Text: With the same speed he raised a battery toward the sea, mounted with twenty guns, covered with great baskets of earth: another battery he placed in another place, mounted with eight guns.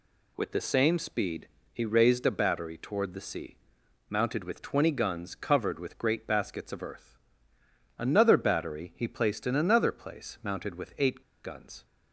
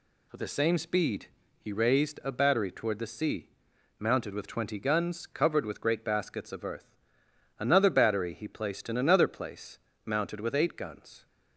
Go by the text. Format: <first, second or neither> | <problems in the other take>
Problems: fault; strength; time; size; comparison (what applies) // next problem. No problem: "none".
second | pauses between "speed" and "he"; slight; at 1.4 s; 0.26 s long; slight in the second // pauses between "eight" and "guns"; slight; at 11.2 s; 0.22 s long